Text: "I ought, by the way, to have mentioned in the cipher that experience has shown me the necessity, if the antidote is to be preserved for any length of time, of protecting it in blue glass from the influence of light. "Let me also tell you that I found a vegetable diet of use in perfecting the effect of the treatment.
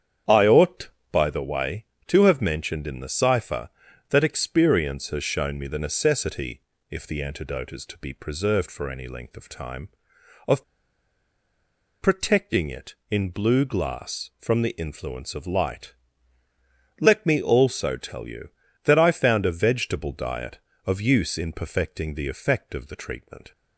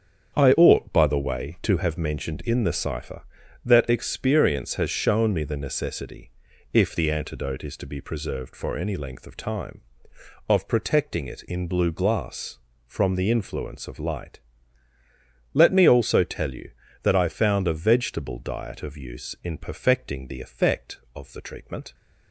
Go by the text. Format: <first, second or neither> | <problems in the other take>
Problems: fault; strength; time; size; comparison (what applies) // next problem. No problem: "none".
second | starts louder than the rest; strong; until 1.5 s; 8.5 dB; strong in the second // pauses between "of" and "protecting"; strong; at 10.6 s; 1.3 s long